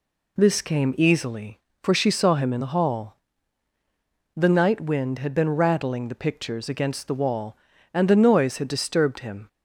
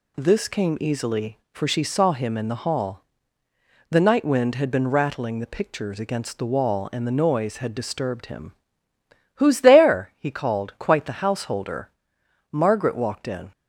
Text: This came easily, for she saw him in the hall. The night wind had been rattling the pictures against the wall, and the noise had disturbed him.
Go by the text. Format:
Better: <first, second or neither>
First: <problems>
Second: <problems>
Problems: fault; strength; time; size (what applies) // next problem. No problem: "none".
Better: first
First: none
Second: goes on to say "Who's there he called quite the householder Margaret walked in"; strong; from 9.3 s on; 4.1 s long